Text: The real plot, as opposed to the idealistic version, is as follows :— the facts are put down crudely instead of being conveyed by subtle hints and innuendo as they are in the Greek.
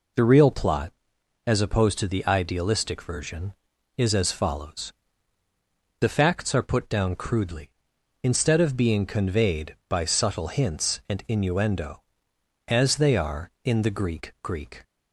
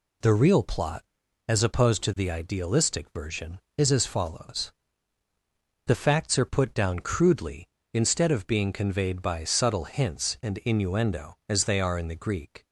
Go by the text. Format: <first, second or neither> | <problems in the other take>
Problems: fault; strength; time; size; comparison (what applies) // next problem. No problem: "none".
second | says "Greek" twice; at 14.4 s